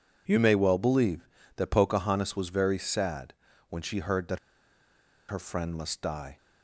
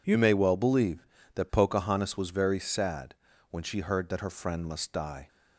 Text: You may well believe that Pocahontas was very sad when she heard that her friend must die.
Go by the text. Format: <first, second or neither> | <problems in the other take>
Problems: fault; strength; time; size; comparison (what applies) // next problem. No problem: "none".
second | pauses between "sad" and "when"; slight; at 3.3 s; 0.36 s long; slight in the second // pauses between "that" and "her"; noticeable; at 4.3 s; 0.92 s long